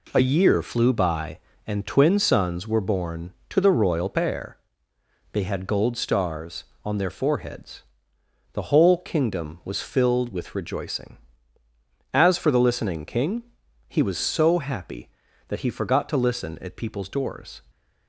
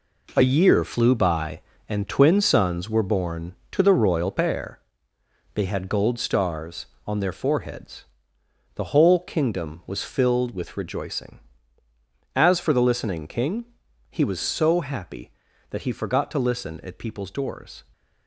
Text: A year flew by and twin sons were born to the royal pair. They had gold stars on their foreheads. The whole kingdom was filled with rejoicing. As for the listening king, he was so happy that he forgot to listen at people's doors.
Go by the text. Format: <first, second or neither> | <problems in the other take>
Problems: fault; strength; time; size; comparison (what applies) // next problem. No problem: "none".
first | gets quieter; strong; throughout; 8 dB